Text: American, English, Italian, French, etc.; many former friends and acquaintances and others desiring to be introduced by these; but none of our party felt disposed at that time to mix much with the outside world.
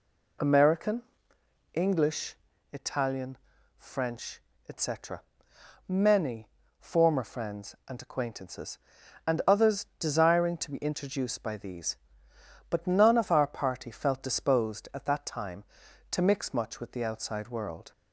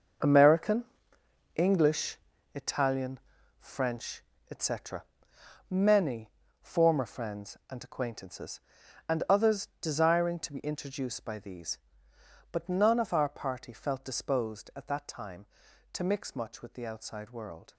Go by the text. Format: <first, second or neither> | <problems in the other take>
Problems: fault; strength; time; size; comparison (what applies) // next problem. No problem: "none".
first | gets quieter; strong; throughout; 11 dB // pauses between "many" and "former"; slight; at 6.2 s; 0.32 s long; slight in the first